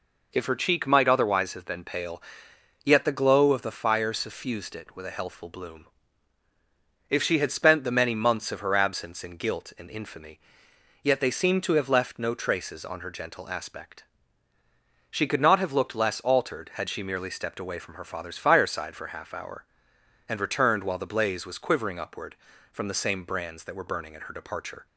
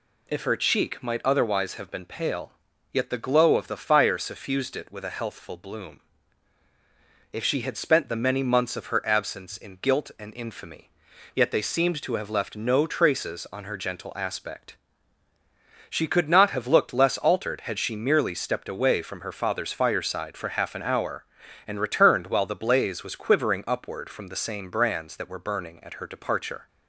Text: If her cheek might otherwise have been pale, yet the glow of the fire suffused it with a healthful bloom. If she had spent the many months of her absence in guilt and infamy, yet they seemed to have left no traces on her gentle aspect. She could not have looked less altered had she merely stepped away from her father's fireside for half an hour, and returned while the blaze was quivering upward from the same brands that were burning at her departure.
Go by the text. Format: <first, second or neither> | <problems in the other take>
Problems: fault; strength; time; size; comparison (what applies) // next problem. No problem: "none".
second | skips "an"; at 19.3 s